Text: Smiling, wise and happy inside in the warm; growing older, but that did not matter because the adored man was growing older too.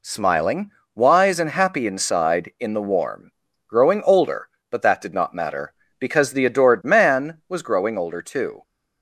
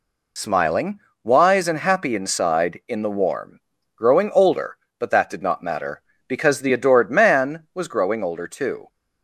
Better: first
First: none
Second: loses the start of "Smiling"; at 0.3 s; 50 ms

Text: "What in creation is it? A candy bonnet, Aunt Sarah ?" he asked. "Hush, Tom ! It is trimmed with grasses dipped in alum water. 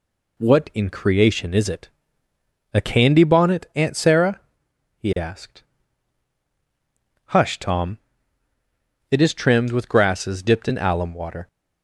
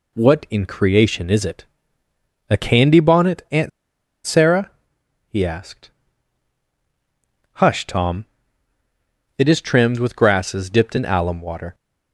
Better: first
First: none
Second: pauses between "Aunt" and "Sarah"; noticeable; at 3.6 s; 0.56 s long

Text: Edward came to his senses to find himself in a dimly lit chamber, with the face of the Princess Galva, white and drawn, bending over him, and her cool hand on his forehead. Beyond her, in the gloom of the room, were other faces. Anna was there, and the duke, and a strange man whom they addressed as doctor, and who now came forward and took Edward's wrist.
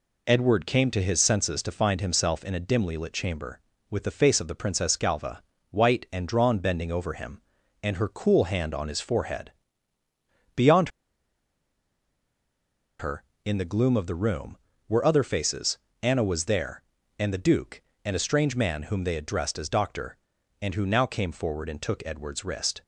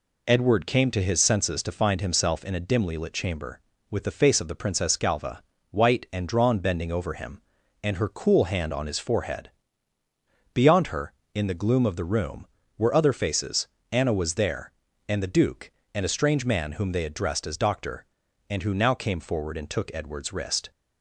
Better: second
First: pauses between "Beyond" and "her"; strong; at 10.8 s; 2.1 s long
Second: none

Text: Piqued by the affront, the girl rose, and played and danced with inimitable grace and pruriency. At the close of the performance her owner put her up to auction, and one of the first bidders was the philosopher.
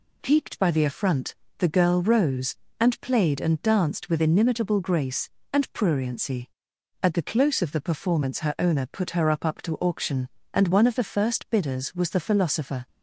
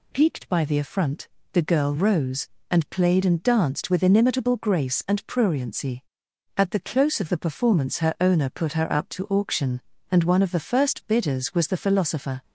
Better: second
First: says "up" twice; at 9.4 s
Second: none

